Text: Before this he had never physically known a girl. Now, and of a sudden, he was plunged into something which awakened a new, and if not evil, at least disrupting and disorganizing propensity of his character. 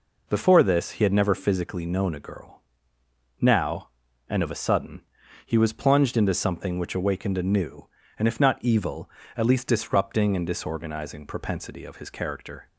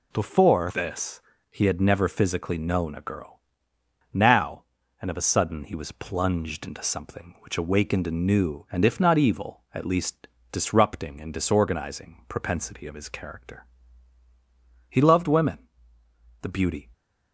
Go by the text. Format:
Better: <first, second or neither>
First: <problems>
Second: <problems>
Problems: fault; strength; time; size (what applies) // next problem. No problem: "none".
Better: first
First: none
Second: pauses between "this" and "he"; slight; at 1.2 s; 0.30 s long // pauses between "least" and "disrupting"; slight; at 10.2 s; 0.24 s long // goes on to say "He loved women the beauty"; strong; from 14.8 s on; 2.0 s long